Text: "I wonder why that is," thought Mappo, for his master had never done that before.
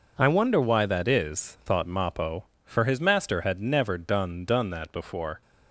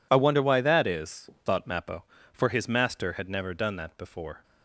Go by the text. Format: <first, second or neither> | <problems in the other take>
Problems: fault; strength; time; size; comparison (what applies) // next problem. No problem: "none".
second | says "done" twice; at 4.4 s